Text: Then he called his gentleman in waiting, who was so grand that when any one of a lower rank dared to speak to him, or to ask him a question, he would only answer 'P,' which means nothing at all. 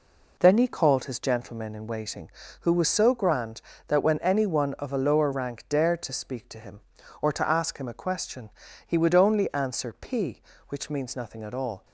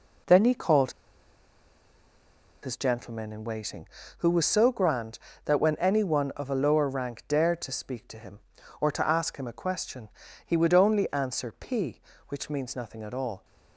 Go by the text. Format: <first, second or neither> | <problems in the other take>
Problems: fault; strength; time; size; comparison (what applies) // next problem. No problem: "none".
first | pauses between "called" and "his"; strong; at 0.9 s; 1.7 s long